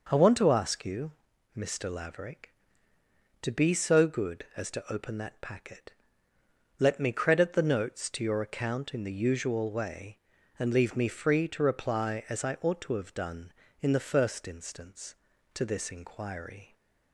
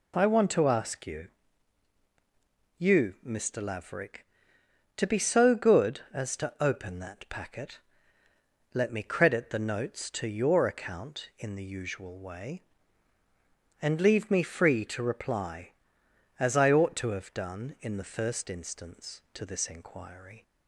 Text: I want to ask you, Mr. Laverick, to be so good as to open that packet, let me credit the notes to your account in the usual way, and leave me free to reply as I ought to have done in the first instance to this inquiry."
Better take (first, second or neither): first